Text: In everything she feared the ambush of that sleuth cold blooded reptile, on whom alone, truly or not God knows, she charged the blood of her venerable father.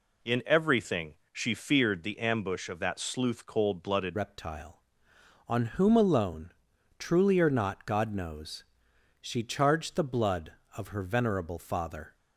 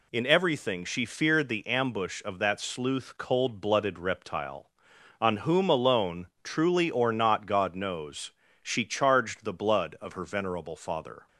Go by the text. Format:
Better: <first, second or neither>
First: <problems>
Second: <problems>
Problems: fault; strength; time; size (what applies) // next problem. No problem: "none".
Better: second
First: pauses between "everything" and "she"; slight; at 1.1 s; 0.18 s long // changes voice at "reptile"; from 4.1 s on; 8.0 s long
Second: none